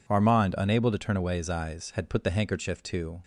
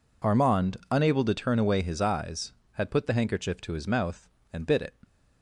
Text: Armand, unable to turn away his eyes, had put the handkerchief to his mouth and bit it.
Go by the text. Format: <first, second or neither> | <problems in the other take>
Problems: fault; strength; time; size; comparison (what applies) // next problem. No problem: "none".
second | stops before "his mouth and bit it"; at 3.2 s